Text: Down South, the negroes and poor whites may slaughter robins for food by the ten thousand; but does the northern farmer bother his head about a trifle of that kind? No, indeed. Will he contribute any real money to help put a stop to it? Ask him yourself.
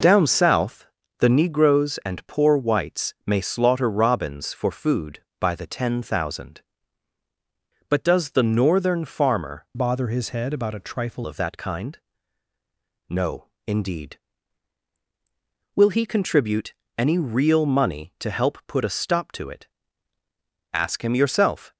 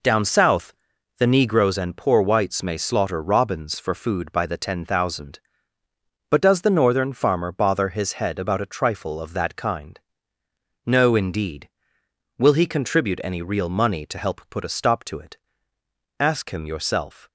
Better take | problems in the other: second | changes voice from "bother" to "trifle"; from 9.7 to 11.2 s; 1.5 s long // pauses between "contribute" and "any"; slight; at 16.7 s; 0.24 s long

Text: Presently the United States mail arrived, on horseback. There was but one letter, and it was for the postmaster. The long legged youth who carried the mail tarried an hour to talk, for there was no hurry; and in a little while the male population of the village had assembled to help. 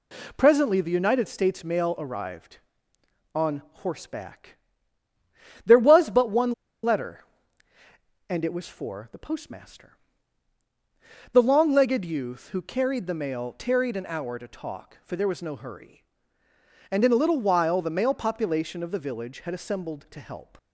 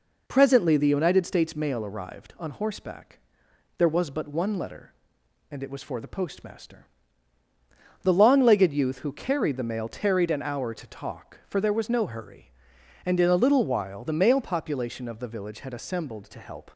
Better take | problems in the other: second | pauses between "one" and "letter"; slight; at 6.5 s; 0.31 s long

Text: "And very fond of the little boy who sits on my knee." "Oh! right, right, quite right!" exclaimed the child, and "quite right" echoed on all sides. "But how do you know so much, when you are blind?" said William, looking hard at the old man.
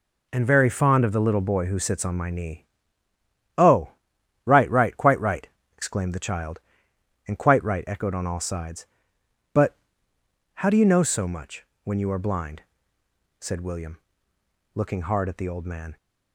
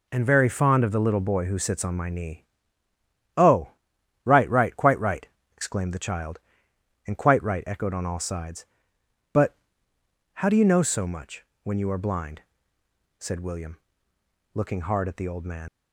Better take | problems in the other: first | pauses between "But" and "how"; noticeable; at 9.5 s; 0.80 s long; noticeable in the first // leaves "man" unfinished; at 15.6 s; 75 ms

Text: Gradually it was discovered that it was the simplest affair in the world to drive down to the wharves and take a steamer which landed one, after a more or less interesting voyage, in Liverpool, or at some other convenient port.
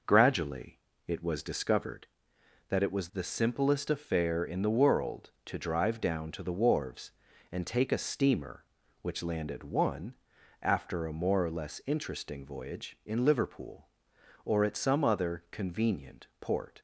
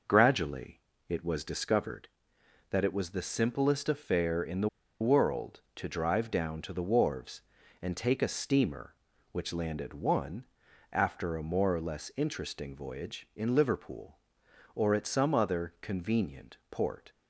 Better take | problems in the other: first | pauses between "Gradually" and "it"; slight; at 0.7 s; 0.30 s long; slight in the first // pauses between "the" and "world"; slight; at 4.6 s; 0.32 s long

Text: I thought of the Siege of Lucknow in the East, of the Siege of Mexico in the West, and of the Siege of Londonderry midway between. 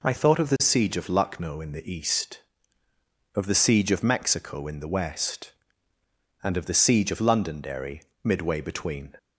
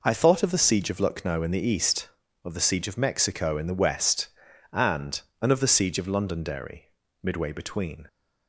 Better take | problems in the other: first | says "and" twice; at 5.4 s // pauses between "Londonderry" and "midway"; slight; at 6.8 s; 0.36 s long; slight in the first

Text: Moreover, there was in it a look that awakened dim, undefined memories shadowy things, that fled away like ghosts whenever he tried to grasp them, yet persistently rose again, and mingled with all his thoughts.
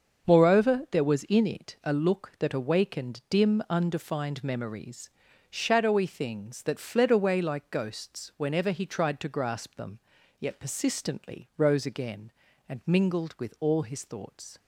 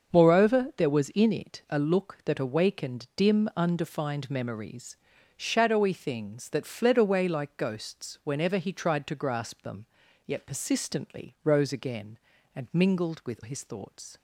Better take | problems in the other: first | starts louder than the rest; until 1.1 s; 6.5 dB; also in the first // pauses between "memories" and "shadowy"; at 4.9 s; 0.40 s long; also in the first // skips "all"; at 13.4 s

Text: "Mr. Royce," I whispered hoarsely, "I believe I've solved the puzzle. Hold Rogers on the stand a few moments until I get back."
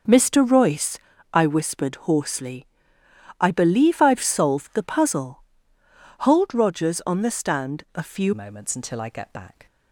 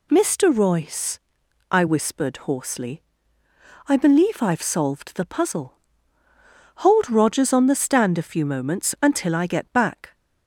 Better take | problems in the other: second | starts louder than the rest; noticeable; until 1.4 s; 6 dB // changes voice at "moments"; from 8.3 s on; 1.3 s long

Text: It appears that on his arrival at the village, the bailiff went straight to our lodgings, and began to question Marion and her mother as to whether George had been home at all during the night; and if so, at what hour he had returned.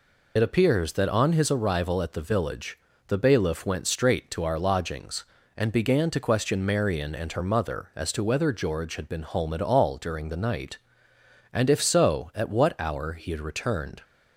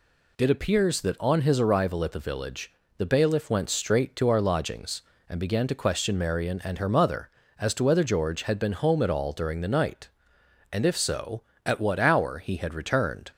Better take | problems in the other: second | loses the start of "It"; at 0.3 s; 35 ms

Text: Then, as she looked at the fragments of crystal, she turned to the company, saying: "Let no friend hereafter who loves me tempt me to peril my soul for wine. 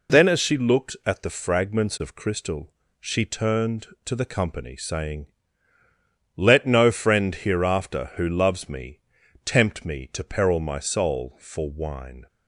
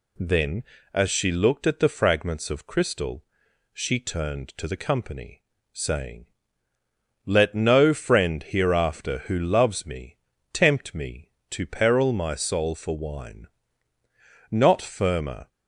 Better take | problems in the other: first | pauses between "me" and "tempt"; at 10.1 s; 0.38 s long; noticeable in the first // goes on to say "Not firmer"; noticeable; from 14.5 s on; 0.98 s long

